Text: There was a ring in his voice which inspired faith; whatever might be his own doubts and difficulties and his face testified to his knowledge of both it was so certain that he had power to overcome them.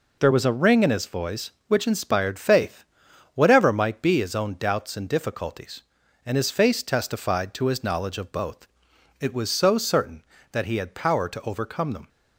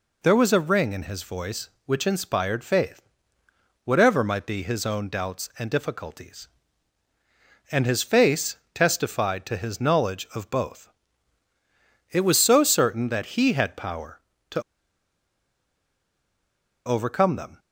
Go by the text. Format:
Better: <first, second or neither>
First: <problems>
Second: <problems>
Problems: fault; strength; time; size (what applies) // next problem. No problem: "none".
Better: first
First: pauses between "both" and "it"; noticeable; at 8.6 s; 0.54 s long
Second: pauses between "face" and "testified"; slight; at 8.5 s; 0.16 s long // pauses between "both" and "it"; at 10.8 s; 1.2 s long // pauses between "to" and "overcome"; strong; at 14.6 s; 2.2 s long